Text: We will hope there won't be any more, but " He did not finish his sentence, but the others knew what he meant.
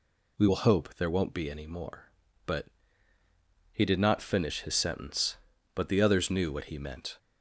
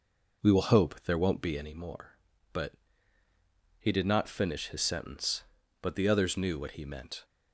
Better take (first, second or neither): first